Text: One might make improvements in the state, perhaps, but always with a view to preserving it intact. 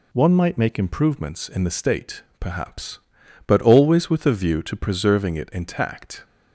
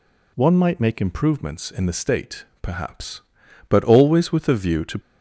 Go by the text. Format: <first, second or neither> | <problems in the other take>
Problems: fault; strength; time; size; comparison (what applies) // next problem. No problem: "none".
first | stops before "preserving it intact"; at 4.9 s